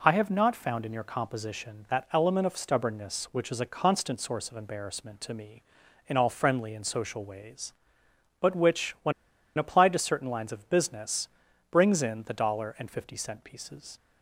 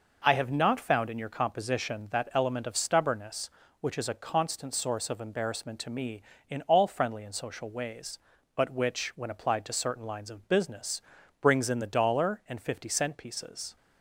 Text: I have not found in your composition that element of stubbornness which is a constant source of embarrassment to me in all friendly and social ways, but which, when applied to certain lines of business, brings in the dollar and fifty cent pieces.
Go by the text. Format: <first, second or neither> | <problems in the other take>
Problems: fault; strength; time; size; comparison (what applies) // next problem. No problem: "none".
second | pauses between "when" and "applied"; at 9.1 s; 0.45 s long